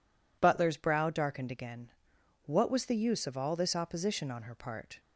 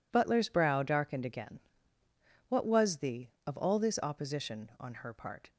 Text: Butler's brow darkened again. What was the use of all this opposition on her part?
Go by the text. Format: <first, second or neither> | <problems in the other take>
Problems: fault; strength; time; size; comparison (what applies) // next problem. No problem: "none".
first | skips "use"; at 3.3 s